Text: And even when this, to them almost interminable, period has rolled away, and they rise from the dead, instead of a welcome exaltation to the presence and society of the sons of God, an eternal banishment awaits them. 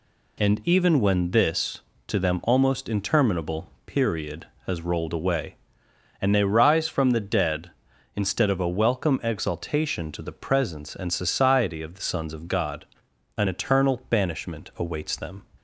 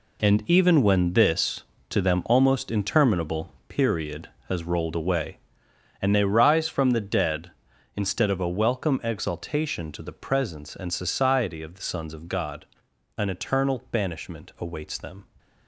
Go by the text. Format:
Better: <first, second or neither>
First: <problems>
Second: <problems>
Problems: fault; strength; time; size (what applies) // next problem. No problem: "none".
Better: first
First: none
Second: gets quieter; strong; throughout; 11 dB